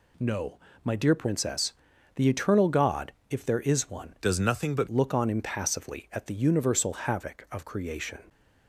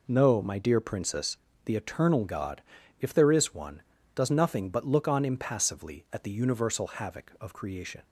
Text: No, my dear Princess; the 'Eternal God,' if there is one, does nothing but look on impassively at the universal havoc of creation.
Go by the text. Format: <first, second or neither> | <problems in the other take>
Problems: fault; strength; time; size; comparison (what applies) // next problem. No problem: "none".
second | changes voice from "does" to "but"; from 4.2 to 4.8 s; 0.6 s long